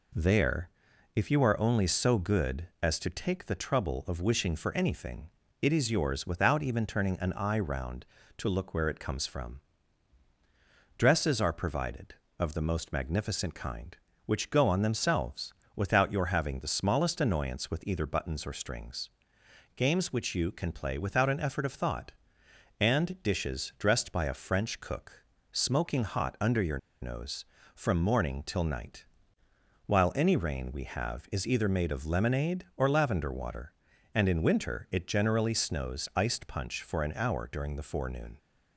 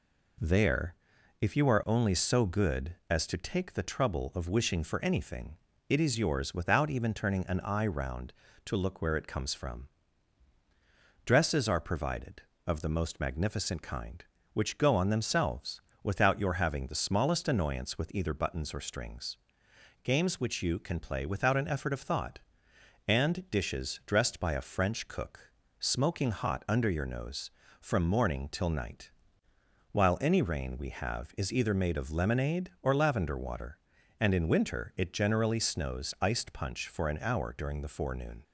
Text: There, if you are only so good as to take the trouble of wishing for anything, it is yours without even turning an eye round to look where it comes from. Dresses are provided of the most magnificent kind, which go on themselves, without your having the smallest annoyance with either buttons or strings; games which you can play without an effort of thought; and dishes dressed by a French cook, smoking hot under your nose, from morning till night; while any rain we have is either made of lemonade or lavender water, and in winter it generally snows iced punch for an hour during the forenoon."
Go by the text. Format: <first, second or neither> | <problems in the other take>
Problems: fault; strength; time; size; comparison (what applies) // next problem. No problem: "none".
second | pauses between "your" and "nose"; slight; at 26.7 s; 0.24 s long